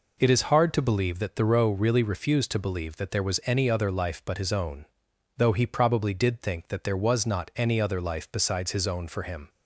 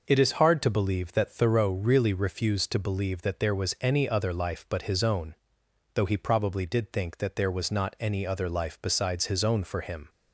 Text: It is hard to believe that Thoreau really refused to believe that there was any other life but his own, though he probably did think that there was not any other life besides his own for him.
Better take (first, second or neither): neither